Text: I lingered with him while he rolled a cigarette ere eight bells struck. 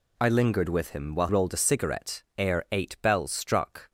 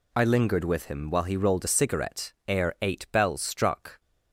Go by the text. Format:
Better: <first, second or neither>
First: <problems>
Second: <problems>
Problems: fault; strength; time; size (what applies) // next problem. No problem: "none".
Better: second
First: skips "he"; at 1.2 s // pauses between "cigarette" and "ere"; slight; at 2.2 s; 0.16 s long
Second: pauses between "cigarette" and "ere"; slight; at 2.3 s; 0.16 s long